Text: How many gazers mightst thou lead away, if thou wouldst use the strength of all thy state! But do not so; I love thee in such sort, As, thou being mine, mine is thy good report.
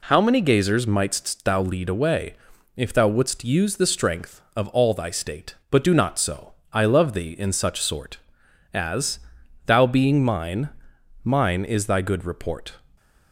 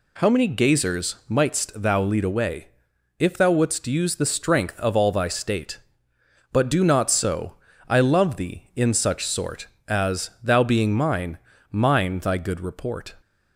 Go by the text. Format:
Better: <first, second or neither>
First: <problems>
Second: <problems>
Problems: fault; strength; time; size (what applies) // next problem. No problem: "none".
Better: first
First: none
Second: skips "is"; at 12.2 s